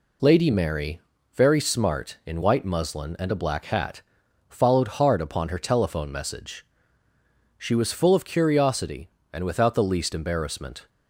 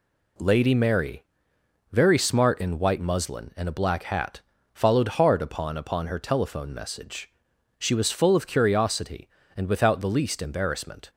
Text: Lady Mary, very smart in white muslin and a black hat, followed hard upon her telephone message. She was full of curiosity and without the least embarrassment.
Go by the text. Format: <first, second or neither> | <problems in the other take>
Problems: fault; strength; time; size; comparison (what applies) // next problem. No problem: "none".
first | says "upon" twice; at 5.7 s